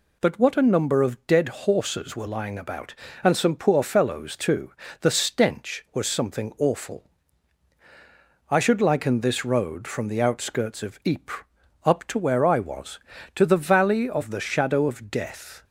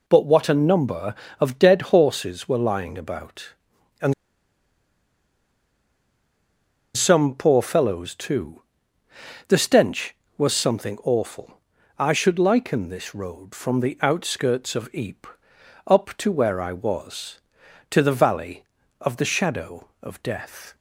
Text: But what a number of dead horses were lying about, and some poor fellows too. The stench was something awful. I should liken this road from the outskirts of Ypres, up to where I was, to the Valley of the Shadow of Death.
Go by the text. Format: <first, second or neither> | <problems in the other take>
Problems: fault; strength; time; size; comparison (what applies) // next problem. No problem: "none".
first | pauses between "and" and "some"; strong; at 4.1 s; 2.8 s long